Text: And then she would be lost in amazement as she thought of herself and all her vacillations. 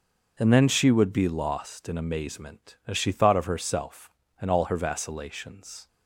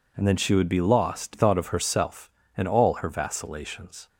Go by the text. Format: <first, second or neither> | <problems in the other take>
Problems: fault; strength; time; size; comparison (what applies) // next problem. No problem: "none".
first | skips "in amazement as she"; at 1.3 s